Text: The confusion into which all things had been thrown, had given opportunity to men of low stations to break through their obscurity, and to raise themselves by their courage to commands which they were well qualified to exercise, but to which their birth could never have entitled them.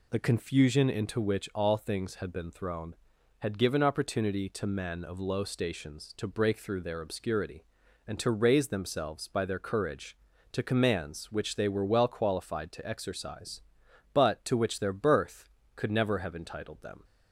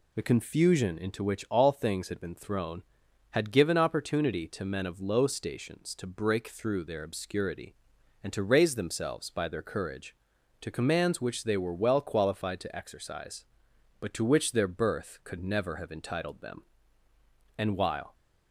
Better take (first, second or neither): first